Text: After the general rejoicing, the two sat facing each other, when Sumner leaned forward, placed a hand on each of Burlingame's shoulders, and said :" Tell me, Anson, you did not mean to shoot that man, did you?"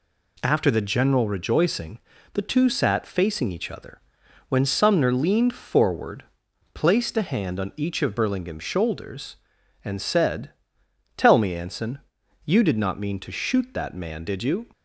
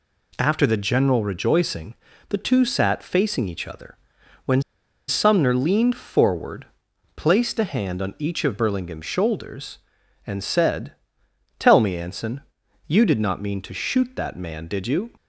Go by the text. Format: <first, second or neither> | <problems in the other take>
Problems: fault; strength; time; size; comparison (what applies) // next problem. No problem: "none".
first | pauses between "when" and "Sumner"; noticeable; at 4.6 s; 0.46 s long